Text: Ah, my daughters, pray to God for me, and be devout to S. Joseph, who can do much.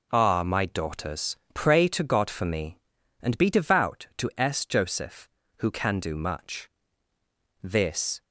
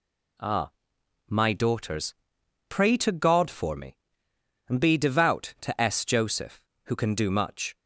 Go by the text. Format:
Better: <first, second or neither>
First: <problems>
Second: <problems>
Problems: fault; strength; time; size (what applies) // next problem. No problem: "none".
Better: second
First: goes on to say "This"; from 7.6 s on; 0.60 s long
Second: none